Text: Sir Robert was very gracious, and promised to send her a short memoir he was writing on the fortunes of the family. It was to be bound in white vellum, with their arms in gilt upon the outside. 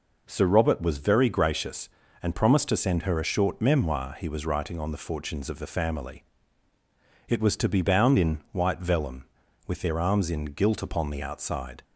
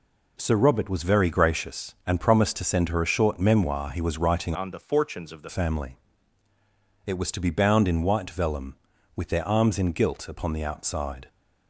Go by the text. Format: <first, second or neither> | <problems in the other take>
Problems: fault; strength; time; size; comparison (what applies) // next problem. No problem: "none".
first | changes voice from "on" to "the"; from 4.5 to 5.4 s; 0.9 s long